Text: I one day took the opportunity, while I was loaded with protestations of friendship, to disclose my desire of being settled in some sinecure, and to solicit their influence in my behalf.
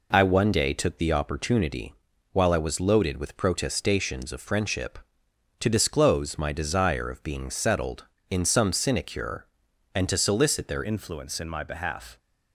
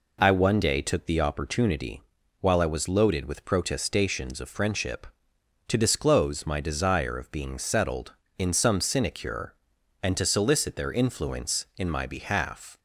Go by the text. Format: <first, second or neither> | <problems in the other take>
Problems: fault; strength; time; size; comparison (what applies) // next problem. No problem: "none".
second | changes voice at "influence"; from 10.8 s on; 1.3 s long